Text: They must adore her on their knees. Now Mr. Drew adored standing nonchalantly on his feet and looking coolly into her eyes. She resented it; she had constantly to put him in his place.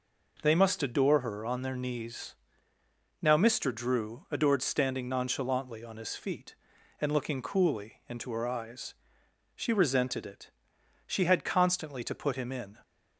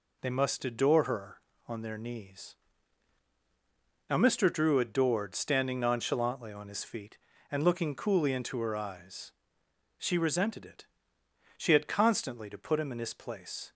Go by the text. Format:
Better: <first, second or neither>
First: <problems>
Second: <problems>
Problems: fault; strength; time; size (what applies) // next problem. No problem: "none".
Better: second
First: stops before "his place"; at 12.8 s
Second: none